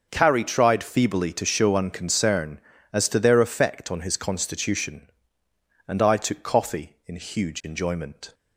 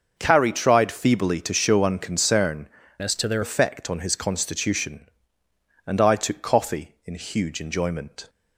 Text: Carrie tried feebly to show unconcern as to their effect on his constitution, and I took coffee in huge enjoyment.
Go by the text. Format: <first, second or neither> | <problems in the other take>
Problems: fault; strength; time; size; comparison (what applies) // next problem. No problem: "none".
first | starts louder than the rest; until 1.1 s; 6 dB; also in the first // changes voice from "as" to "their"; from 2.9 to 3.4 s; 0.5 s long